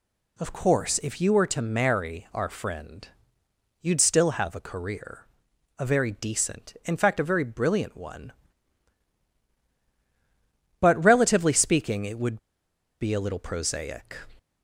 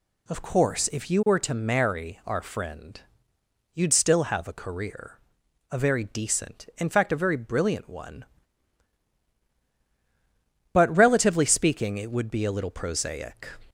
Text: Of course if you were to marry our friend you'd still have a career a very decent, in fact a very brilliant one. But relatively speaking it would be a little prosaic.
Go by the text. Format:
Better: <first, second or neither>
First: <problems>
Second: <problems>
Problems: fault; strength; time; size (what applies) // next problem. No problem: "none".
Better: second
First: pauses between "friend" and "you'd"; noticeable; at 3.0 s; 0.72 s long // pauses between "career" and "a"; noticeable; at 5.2 s; 0.56 s long // pauses between "would" and "be"; noticeable; at 12.3 s; 0.62 s long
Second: pauses between "friend" and "you'd"; noticeable; at 3.0 s; 0.72 s long // pauses between "career" and "a"; noticeable; at 5.1 s; 0.56 s long